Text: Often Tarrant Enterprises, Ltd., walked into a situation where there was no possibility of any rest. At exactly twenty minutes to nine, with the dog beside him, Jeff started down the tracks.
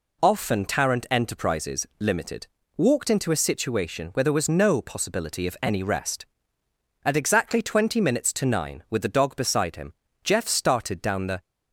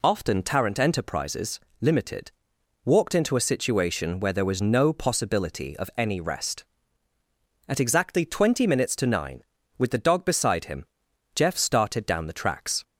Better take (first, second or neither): second